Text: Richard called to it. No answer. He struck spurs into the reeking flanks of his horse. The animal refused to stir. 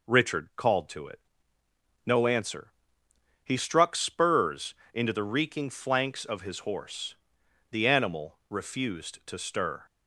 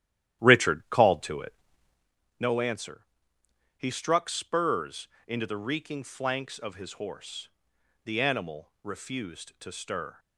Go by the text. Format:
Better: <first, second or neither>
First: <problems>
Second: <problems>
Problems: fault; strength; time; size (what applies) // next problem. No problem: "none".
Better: first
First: pauses between "spurs" and "into"; slight; at 4.7 s; 0.20 s long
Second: starts louder than the rest; strong; until 2.2 s; 12.5 dB // pauses between "spurs" and "into"; slight; at 5.0 s; 0.20 s long